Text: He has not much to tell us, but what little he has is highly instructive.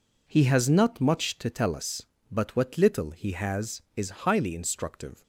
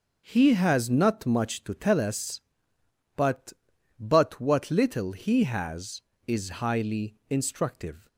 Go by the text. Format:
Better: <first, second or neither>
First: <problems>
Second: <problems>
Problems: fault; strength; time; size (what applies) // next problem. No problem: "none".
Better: first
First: none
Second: says "but" twice; at 3.9 s